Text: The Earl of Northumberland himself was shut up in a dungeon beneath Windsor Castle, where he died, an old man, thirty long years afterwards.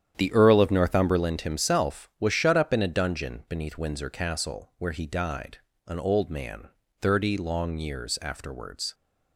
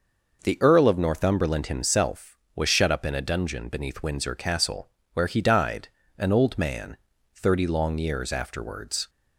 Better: second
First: starts louder than the rest; strong; until 1.4 s; 9.5 dB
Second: none

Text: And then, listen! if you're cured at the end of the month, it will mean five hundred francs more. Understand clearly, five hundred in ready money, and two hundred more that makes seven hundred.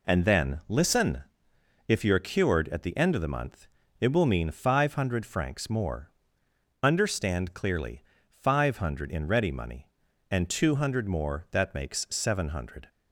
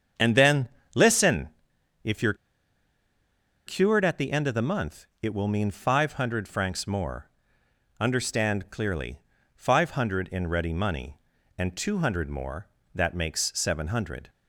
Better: first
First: none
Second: starts louder than the rest; strong; until 1.4 s; 7.5 dB // pauses between "you're" and "cured"; strong; at 2.3 s; 1.3 s long

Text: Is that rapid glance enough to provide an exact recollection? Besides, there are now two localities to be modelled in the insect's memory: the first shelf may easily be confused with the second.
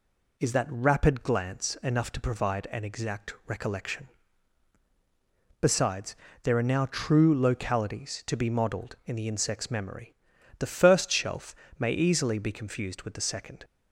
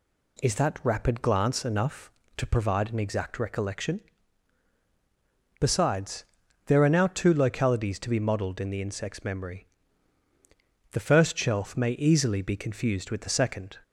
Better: second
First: says "true" for "two"; at 6.8 s // pauses between "shelf" and "may"; slight; at 11.5 s; 0.24 s long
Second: none

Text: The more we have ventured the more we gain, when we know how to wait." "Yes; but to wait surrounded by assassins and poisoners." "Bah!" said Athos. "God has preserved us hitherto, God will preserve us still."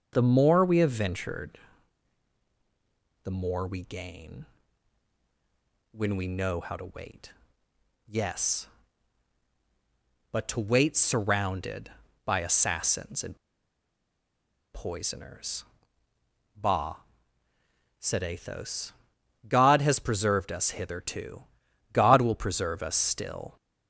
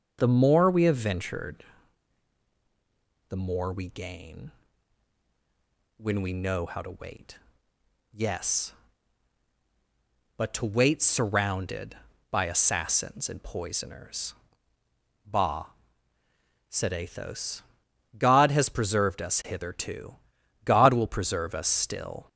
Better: second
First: starts louder than the rest; until 1.1 s; 6.5 dB // pauses between "ventured" and "the"; strong; at 1.5 s; 1.6 s long // pauses between "and" and "poisoners"; strong; at 13.3 s; 1.3 s long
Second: starts louder than the rest; until 1.2 s; 6.5 dB // pauses between "ventured" and "the"; strong; at 1.6 s; 1.6 s long

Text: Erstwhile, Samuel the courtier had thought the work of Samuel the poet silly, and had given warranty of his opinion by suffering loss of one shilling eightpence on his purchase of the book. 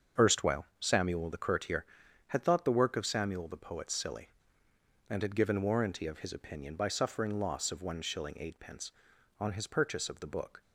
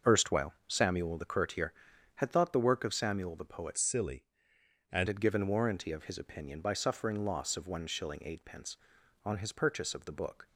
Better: first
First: starts louder than the rest; until 1.3 s; 6.5 dB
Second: starts louder than the rest; noticeable; until 1.2 s; 6 dB // changes voice from "silly" to "and"; from 3.7 to 5.0 s; 1.3 s long

